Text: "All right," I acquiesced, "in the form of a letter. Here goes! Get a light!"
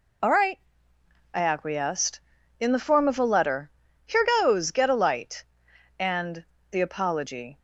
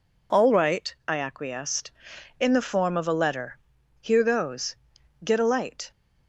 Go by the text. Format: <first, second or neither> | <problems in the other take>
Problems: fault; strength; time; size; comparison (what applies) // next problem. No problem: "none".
second | pauses between "Here" and "goes"; slight; at 4.2 s; 0.16 s long // goes on to say "And the apology"; from 6.0 s on; 1.5 s long